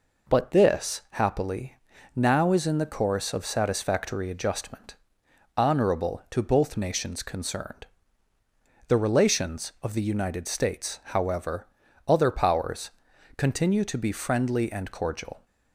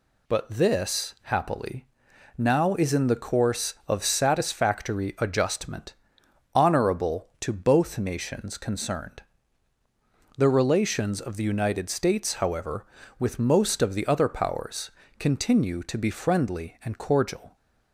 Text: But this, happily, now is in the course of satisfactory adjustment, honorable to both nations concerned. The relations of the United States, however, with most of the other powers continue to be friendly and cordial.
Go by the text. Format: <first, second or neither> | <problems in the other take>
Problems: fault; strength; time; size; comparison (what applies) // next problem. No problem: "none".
second | skips "with most of the"; at 11.8 s // pauses between "powers" and "continue"; noticeable; at 12.9 s; 0.46 s long; slight in the second